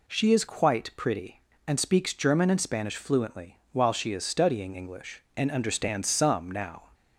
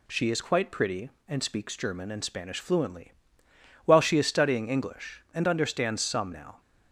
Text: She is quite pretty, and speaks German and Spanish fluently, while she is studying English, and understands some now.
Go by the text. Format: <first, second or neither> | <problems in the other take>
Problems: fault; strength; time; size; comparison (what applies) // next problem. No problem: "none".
neither | none